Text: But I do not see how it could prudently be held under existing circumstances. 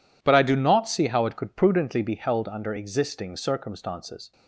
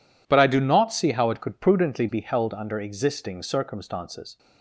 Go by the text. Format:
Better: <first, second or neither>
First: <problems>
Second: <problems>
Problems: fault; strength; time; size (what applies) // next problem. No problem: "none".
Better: neither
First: none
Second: none